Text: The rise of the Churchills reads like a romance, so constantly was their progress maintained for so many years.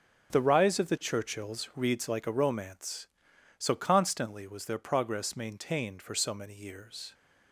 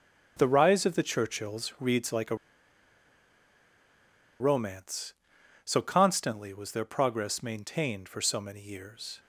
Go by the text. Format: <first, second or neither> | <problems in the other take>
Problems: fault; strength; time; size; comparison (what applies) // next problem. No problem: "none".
first | starts louder than the rest; until 1.3 s; 6.5 dB; strong in the first // pauses between "a" and "romance"; strong; at 2.3 s; 2.0 s long